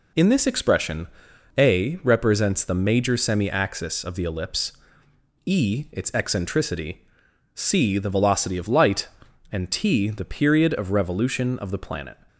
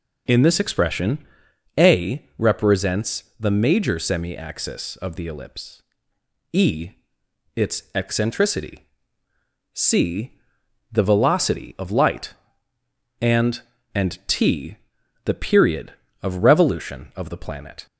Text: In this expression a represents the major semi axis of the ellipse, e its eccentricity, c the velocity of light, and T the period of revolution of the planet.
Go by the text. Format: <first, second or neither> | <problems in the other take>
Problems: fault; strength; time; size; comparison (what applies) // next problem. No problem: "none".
first | pauses between "expression" and "a"; noticeable; at 1.1 s; 0.60 s long; noticeable in the first // pauses between "represents" and "the"; slight; at 3.2 s; 0.16 s long // pauses between "e" and "its"; noticeable; at 6.8 s; 0.64 s long // pauses between "c" and "the"; noticeable; at 10.3 s; 0.60 s long // says "and" twice; at 13.9 s // pauses between "T" and "the"; noticeable; at 14.7 s; 0.48 s long